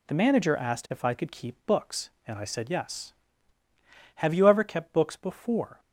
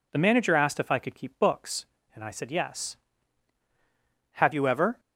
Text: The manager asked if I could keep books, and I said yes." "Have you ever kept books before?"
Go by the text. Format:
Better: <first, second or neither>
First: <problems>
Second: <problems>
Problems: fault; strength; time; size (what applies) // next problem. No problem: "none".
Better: first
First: none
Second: stops before "kept books before"; at 4.9 s